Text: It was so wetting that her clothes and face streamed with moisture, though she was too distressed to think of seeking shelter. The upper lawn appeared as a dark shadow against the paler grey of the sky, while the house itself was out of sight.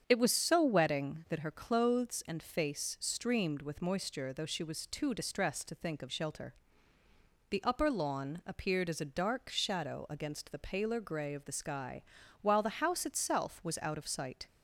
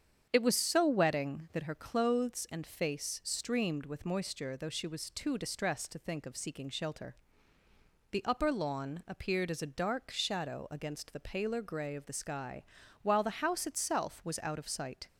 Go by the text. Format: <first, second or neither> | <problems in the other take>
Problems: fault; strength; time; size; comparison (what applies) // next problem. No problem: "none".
second | starts louder than the rest; strong; until 1.0 s; 7.5 dB; strong in the second // skips "seeking"; at 6.0 s